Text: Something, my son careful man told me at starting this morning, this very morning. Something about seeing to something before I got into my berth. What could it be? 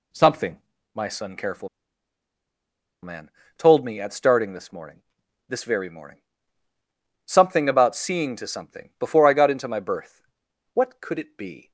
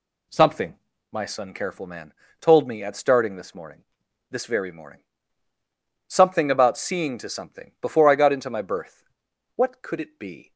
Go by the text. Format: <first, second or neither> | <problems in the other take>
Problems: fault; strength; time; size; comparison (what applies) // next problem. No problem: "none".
second | pauses between "careful" and "man"; strong; at 1.6 s; 1.3 s long // pauses between "man" and "told"; slight; at 3.3 s; 0.26 s long; slight in the second